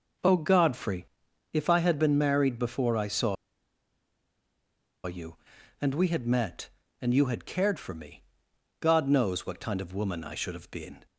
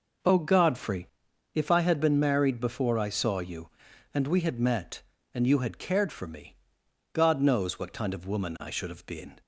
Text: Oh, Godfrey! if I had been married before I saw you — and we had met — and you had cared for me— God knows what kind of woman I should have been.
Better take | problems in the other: second | pauses between "saw" and "you"; strong; at 3.3 s; 1.7 s long

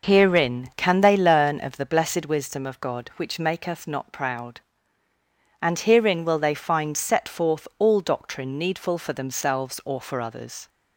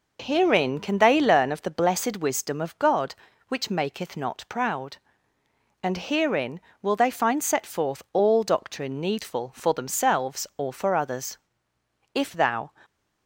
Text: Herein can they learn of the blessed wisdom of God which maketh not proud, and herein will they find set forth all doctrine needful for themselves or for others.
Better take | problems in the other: first | goes on to say "If thou"; from 12.1 s on; 0.56 s long

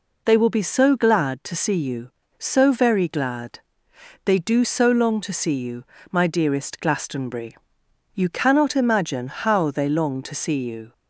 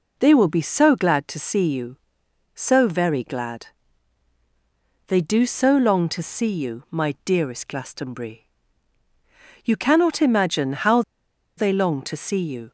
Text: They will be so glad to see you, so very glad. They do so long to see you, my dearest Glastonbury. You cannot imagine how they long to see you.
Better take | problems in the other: first | pauses between "how" and "they"; noticeable; at 11.0 s; 0.56 s long

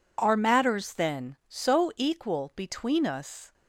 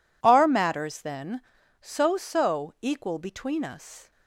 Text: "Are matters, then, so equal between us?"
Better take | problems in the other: first | says "so" twice; at 2.1 s

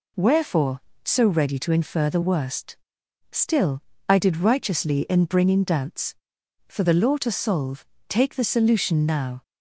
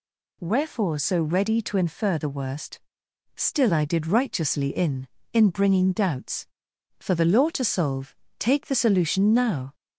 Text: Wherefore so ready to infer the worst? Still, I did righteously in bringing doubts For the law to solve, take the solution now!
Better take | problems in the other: first | says "in" twice; at 5.3 s

